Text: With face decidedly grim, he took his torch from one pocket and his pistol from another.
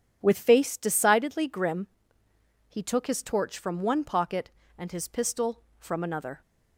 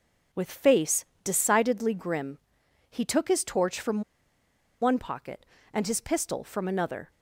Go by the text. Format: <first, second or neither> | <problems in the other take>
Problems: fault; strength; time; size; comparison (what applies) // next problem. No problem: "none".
first | pauses between "face" and "decidedly"; slight; at 1.0 s; 0.20 s long // pauses between "from" and "one"; noticeable; at 4.0 s; 0.79 s long